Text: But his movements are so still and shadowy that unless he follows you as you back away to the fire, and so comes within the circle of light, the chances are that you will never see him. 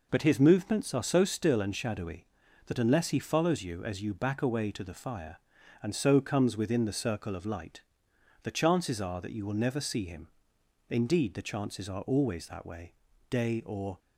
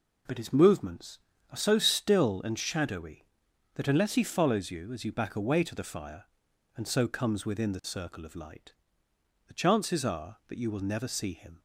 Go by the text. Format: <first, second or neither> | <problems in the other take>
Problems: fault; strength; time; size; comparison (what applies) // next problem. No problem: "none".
second | goes on to say "Indeed the chances are always that way day or"; strong; from 10.8 s on; 3.0 s long